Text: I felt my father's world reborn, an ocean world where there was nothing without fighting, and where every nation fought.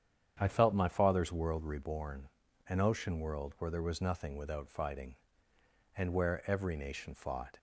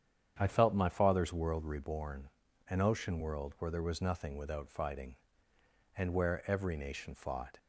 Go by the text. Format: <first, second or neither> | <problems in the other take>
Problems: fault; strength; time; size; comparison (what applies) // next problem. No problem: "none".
neither | starts louder than the rest; strong; the same in both